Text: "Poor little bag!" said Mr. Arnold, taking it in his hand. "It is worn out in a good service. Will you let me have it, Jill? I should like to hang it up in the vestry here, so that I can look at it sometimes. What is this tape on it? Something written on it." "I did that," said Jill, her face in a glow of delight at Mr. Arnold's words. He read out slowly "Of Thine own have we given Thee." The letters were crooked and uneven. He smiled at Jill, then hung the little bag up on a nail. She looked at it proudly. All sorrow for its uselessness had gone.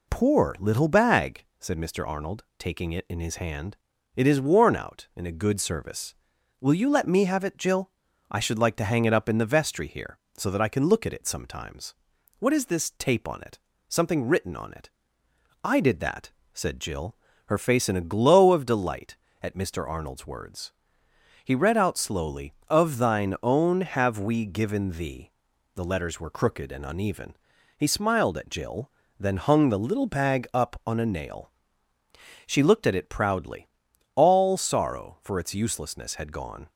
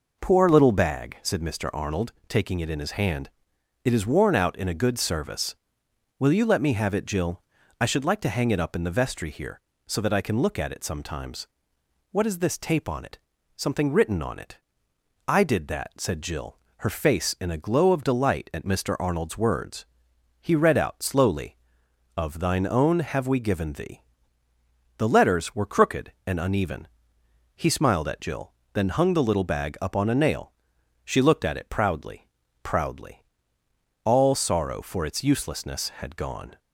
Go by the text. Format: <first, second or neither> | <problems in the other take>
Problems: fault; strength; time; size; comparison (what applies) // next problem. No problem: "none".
first | says "proudly" twice; at 32.6 s